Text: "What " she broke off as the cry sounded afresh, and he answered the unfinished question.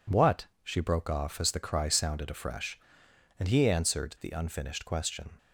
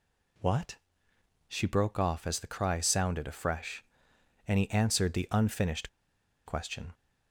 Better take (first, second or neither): first